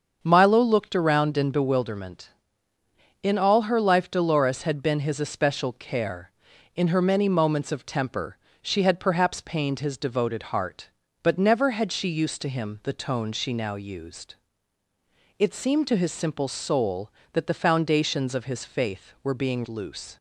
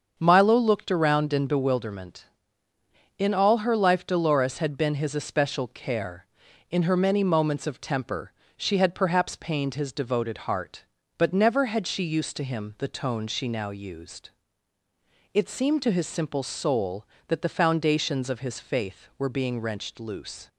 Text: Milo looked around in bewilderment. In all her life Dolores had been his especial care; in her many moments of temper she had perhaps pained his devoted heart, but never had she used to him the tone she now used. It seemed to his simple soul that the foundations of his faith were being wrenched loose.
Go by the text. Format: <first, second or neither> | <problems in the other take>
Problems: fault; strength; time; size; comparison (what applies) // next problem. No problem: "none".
second | starts louder than the rest; until 1.2 s; 7 dB; also in the second // pauses between "temper" and "she"; slight; at 8.3 s; 0.26 s long; slight in the second // skips "wrenched"; at 19.6 s